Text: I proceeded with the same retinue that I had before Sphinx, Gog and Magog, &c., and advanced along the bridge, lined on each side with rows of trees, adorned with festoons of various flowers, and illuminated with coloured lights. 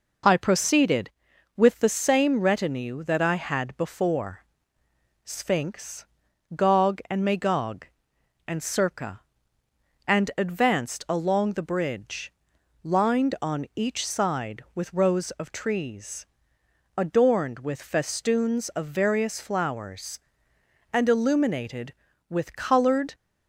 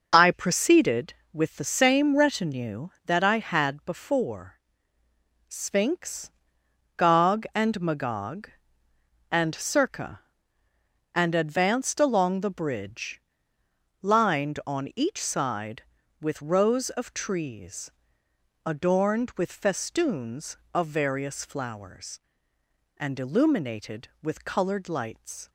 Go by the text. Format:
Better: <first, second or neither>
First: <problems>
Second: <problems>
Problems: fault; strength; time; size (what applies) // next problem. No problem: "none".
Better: second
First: pauses between "before" and "Sphinx"; noticeable; at 4.3 s; 0.88 s long // stops before "lights"; at 23.1 s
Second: pauses between "before" and "Sphinx"; noticeable; at 4.5 s; 0.88 s long